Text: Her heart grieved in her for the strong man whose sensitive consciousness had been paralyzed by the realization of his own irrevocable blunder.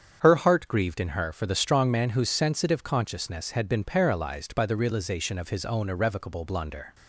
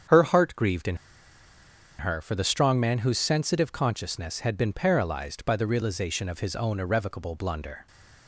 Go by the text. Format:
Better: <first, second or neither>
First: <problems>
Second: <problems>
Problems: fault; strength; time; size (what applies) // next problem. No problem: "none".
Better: first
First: starts louder than the rest; strong; until 1.2 s; 7.5 dB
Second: starts louder than the rest; strong; until 2.1 s; 7.5 dB // pauses between "in" and "her"; at 0.9 s; 1.0 s long